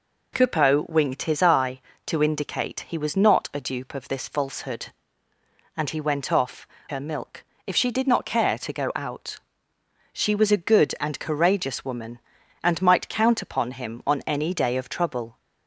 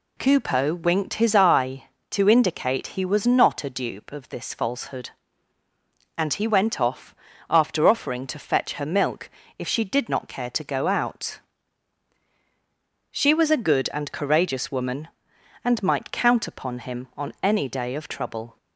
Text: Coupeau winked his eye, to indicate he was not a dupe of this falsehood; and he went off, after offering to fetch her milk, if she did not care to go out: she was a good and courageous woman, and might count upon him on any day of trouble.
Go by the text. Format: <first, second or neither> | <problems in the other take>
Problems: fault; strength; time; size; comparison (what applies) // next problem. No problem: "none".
second | skips "after offering to fetch"; at 6.7 s